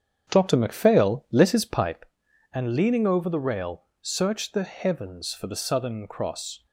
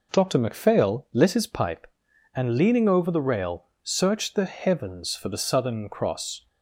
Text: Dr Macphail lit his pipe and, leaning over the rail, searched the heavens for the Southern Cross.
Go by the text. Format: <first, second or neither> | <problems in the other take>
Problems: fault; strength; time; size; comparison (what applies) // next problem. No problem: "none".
second | starts louder than the rest; strong; until 2.2 s; 8 dB